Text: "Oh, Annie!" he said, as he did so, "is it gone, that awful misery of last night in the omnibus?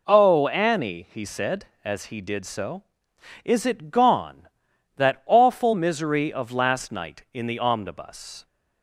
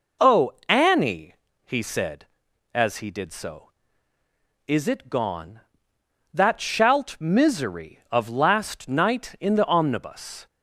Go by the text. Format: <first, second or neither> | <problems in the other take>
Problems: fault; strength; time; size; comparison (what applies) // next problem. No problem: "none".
first | says "shalt" for "awful"; at 6.6 s